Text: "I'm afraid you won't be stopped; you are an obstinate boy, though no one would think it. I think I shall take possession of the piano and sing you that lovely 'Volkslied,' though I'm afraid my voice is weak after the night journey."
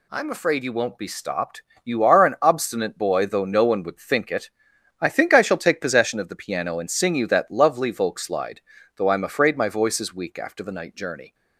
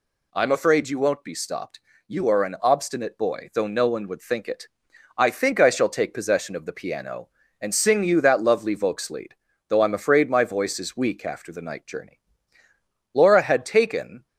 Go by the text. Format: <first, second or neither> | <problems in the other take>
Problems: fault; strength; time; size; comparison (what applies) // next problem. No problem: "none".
first | goes on to say "Laura had taken"; noticeable; from 13.1 s on; 1.1 s long